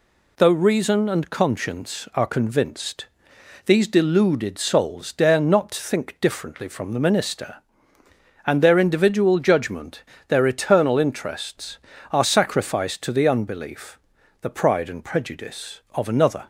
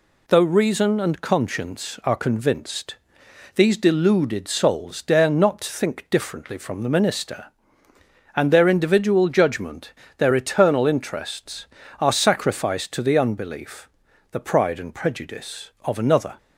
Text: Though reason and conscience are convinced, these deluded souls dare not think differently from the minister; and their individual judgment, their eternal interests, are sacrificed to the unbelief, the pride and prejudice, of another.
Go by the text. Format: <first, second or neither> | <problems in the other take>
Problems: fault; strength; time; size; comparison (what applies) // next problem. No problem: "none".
neither | none